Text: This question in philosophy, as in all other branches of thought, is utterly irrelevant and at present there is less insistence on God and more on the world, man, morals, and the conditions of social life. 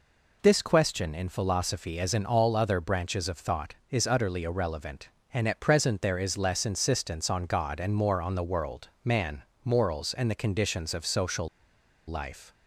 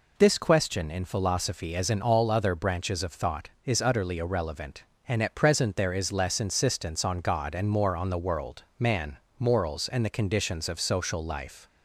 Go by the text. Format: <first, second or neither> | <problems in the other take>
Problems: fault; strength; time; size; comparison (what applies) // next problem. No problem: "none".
second | pauses between "social" and "life"; noticeable; at 11.4 s; 0.62 s long